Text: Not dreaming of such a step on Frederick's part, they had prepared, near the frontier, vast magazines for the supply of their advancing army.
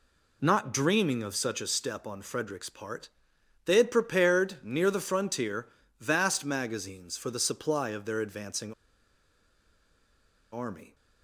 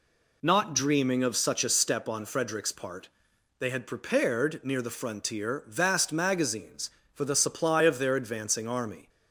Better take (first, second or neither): second